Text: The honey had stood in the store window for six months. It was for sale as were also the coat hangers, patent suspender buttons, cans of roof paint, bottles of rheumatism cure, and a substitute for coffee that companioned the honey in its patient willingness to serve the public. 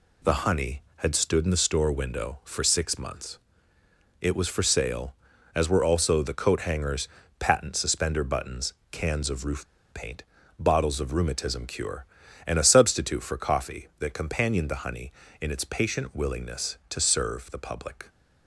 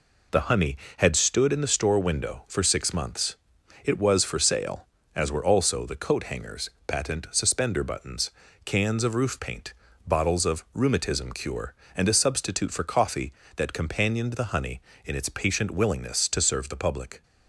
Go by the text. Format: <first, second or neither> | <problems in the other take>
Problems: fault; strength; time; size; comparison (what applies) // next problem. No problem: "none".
second | pauses between "roof" and "paint"; slight; at 9.6 s; 0.26 s long